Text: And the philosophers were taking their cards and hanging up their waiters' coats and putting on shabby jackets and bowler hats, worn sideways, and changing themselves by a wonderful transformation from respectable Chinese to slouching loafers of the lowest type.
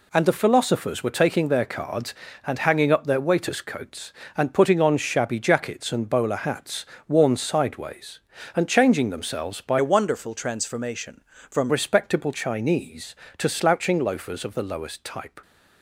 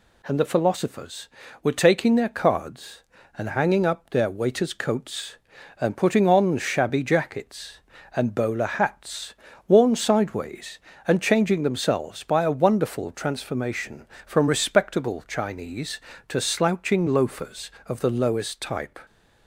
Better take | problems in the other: second | changes voice from "a" to "from"; from 9.7 to 11.7 s; 2.0 s long

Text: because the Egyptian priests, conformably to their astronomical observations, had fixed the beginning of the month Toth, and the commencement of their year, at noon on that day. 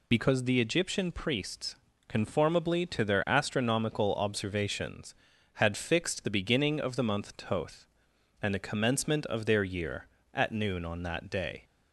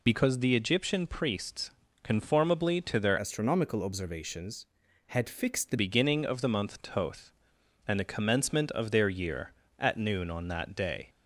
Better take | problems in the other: first | changes voice from "astronomical" to "the"; from 3.1 to 5.7 s; 2.6 s long

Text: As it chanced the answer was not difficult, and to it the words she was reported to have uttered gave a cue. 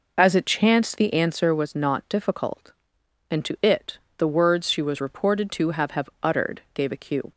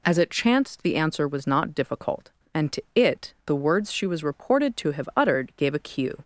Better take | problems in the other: second | pauses between "it" and "the"; slight; at 3.9 s; 0.18 s long // says "have" twice; at 5.9 s

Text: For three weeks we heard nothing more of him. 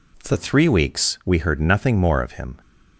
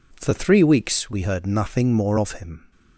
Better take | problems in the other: second | changes voice at "three"; from 0.3 s on; 2.3 s long

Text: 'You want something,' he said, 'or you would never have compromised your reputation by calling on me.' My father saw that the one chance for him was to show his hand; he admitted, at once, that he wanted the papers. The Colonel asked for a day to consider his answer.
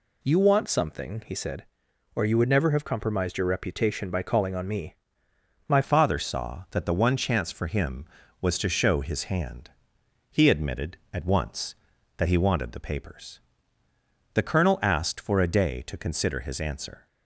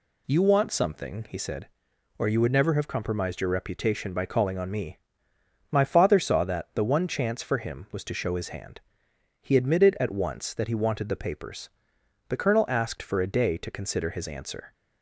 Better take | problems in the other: second | changes voice at "father"; from 5.8 s on; 11.2 s long

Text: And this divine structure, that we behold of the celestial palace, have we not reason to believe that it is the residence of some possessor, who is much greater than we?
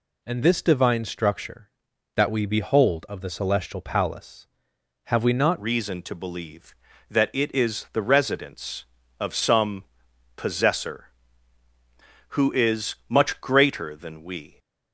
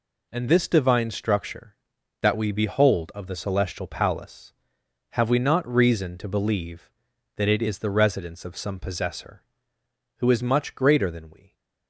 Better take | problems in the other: second | changes voice at "reason"; from 5.6 s on; 8.9 s long // pauses between "some" and "possessor"; noticeable; at 9.8 s; 0.54 s long

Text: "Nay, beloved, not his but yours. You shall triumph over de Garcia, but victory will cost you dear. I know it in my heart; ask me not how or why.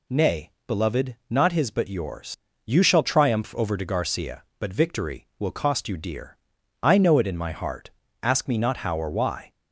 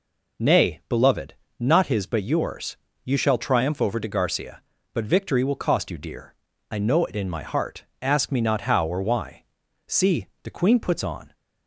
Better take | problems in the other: first | goes on to say "See the Queen puts on"; from 9.8 s on; 1.4 s long

